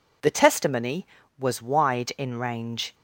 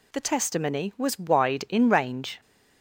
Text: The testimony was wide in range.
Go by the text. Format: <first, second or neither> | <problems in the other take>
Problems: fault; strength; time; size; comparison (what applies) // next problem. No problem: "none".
neither | none